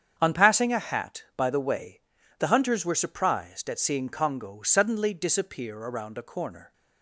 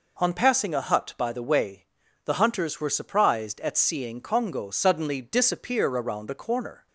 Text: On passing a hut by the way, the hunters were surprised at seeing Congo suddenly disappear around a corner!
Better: second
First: starts louder than the rest; strong; until 1.1 s; 8 dB // says "hat" for "hut"; at 0.7 s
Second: none

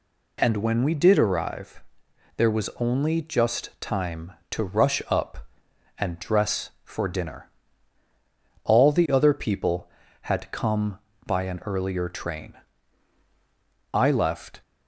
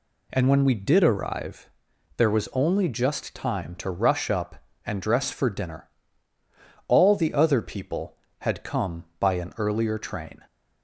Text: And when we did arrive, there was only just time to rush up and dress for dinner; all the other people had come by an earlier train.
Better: second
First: goes on to say "I left"; noticeable; from 13.9 s on; 0.68 s long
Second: none

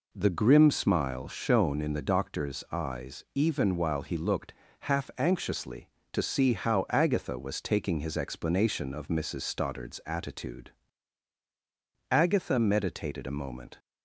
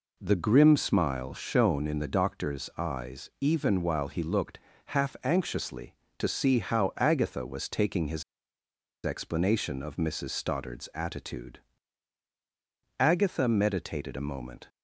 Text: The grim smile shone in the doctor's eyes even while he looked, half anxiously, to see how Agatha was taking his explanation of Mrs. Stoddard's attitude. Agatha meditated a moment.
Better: first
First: none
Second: pauses between "his" and "explanation"; noticeable; at 8.2 s; 0.81 s long

